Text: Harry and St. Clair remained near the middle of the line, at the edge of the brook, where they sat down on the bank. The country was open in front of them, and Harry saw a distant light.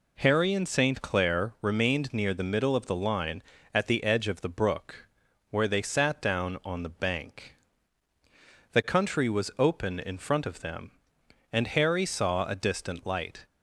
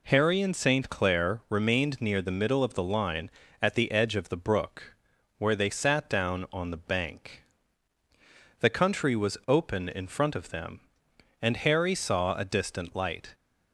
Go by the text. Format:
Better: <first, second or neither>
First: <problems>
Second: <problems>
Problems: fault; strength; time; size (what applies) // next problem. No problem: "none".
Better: neither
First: none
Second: none